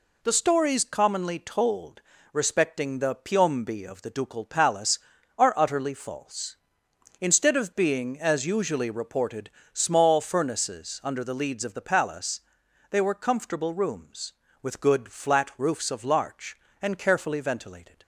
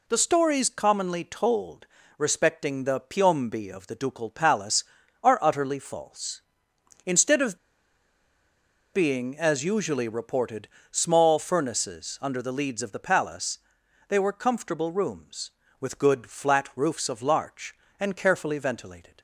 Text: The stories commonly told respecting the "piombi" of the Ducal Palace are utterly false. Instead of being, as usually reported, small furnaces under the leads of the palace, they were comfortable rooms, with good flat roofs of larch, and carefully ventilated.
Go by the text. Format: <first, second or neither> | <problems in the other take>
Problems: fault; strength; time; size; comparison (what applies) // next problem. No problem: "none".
first | pauses between "told" and "respecting"; slight; at 1.8 s; 0.30 s long; slight in the first // pauses between "of" and "being"; strong; at 7.5 s; 1.3 s long